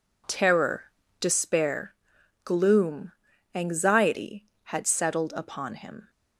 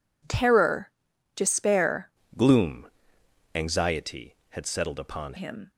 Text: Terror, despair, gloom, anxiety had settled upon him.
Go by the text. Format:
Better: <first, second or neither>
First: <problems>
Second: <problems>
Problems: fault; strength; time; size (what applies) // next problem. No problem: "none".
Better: first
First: none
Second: changes voice from "gloom" to "upon"; from 2.3 to 5.3 s; 3.0 s long